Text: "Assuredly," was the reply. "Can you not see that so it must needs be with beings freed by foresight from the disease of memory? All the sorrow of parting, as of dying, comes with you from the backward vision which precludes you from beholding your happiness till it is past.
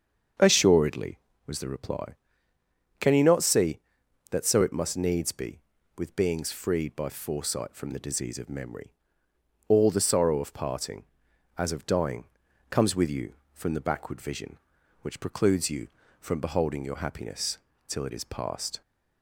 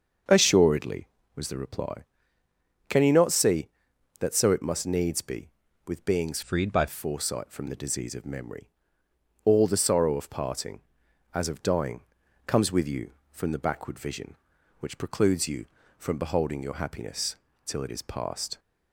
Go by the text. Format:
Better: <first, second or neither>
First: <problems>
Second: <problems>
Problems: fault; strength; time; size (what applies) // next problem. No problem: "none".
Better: first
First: starts louder than the rest; until 1.6 s; 7 dB // pauses between "happiness" and "till"; slight; at 17.5 s; 0.30 s long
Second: starts louder than the rest; until 1.5 s; 6.5 dB // changes voice from "freed" to "by"; from 6.4 to 6.8 s; 0.4 s long // pauses between "happiness" and "till"; slight; at 17.3 s; 0.30 s long